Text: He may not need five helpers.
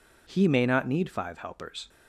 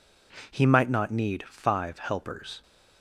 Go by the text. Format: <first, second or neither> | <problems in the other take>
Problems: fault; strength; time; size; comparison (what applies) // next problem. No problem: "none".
first | says "might" for "may"; at 0.6 s